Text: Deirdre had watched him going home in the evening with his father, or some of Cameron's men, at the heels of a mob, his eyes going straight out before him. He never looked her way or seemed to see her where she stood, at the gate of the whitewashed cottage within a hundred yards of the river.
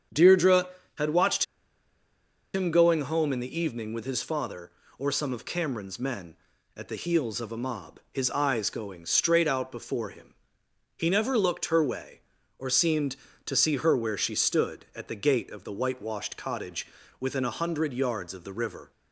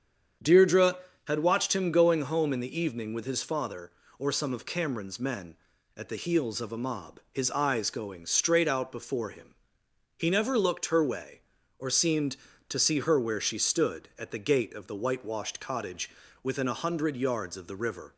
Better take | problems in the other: second | starts louder than the rest; strong; until 1.4 s; 8 dB; strong in the second // pauses between "watched" and "him"; at 1.4 s; 1.0 s long // pauses between "cottage" and "within"; slight; at 16.8 s; 0.34 s long; slight in the second

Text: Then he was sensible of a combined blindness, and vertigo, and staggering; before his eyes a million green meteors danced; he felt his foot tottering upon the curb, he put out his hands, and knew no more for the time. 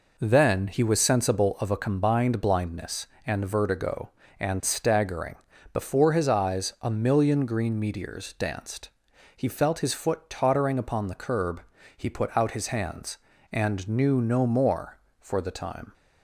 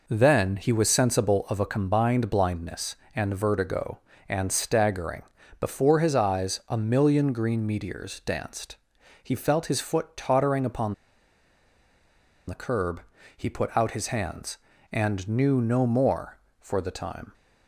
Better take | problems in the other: first | pauses between "upon" and "the"; strong; at 10.9 s; 1.5 s long

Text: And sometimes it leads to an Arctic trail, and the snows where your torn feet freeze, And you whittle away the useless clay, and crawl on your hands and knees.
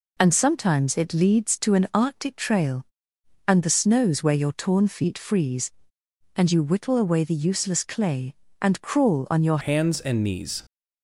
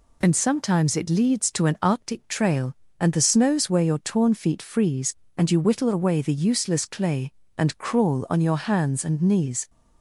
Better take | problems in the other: second | changes voice at "hands"; from 9.5 s on; 1.1 s long

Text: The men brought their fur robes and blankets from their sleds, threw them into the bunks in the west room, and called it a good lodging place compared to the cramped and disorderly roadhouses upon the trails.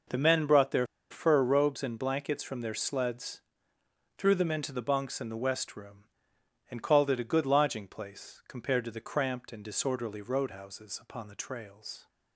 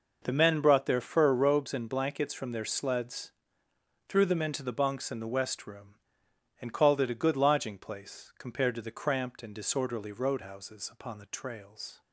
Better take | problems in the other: second | pauses between "their" and "fur"; slight; at 0.8 s; 0.24 s long

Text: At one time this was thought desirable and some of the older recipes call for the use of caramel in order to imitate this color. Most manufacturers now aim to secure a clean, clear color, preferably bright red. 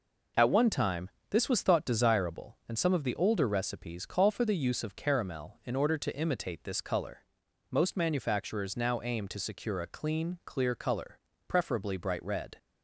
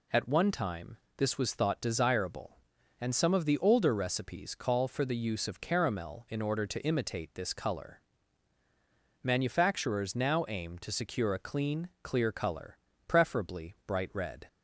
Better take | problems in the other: first | pauses between "time" and "this"; slight; at 0.9 s; 0.20 s long; slight in the first // skips "Most"; at 8.6 s

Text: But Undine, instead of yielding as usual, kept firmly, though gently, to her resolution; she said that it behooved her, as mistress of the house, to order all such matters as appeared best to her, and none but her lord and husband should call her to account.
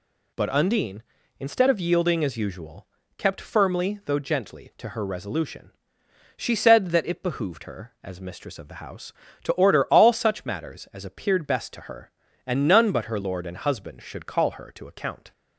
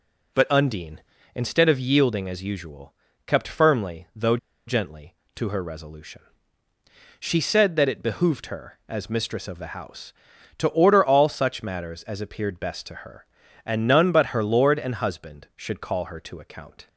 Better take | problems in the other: first | pauses between "though" and "gently"; slight; at 4.3 s; 0.30 s long

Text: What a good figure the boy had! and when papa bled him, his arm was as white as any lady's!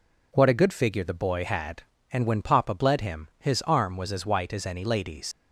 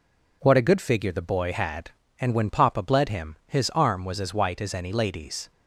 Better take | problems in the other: second | leaves "lady's" unfinished; at 5.3 s; 110 ms

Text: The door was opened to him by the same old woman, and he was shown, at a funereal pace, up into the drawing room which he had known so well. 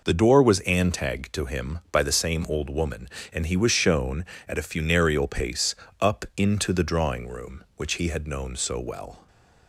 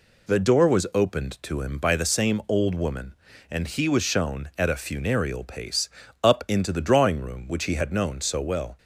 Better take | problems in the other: second | says "antag" for "opened"; at 0.6 s // stays silent after the last word; slight; from 9.1 s on; 0.5 s long

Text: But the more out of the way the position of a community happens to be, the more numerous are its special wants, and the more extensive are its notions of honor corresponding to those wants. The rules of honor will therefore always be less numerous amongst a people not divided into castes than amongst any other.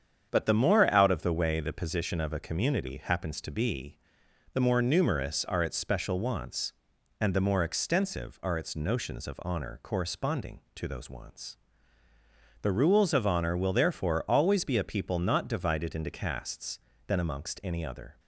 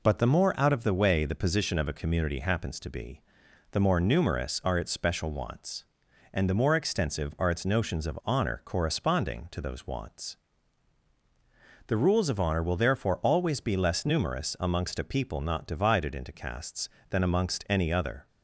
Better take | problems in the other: second | starts louder than the rest; strong; until 1.3 s; 8 dB // skips "less numerous amongst"; at 14.7 s

